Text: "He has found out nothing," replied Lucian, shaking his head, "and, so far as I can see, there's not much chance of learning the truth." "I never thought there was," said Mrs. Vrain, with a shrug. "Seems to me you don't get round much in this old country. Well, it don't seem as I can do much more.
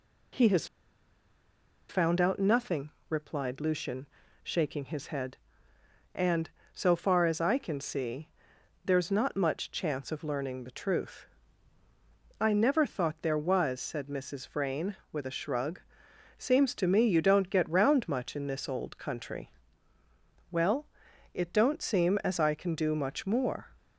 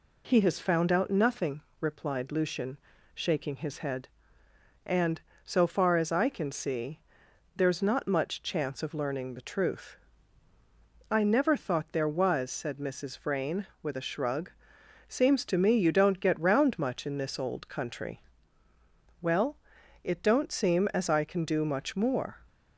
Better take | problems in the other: second | pauses between "has" and "found"; at 0.6 s; 1.2 s long

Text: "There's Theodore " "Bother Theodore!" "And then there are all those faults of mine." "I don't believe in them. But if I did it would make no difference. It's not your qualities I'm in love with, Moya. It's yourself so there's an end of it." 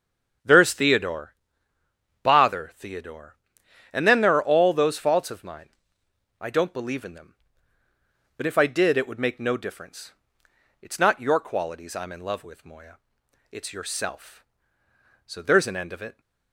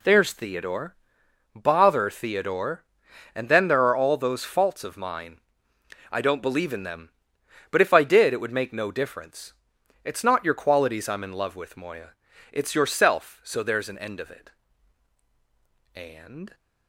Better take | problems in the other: first | goes on to say "And"; from 15.9 s on; 0.60 s long

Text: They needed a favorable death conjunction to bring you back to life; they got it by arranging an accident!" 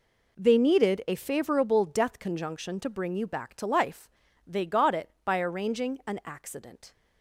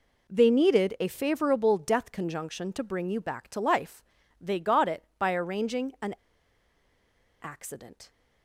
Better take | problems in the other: first | pauses between "an" and "accident"; strong; at 6.1 s; 1.2 s long

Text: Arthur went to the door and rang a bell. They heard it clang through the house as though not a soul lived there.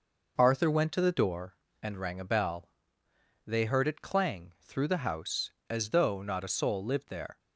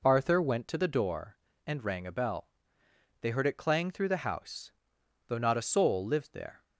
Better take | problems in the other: first | skips "as"; at 5.0 s

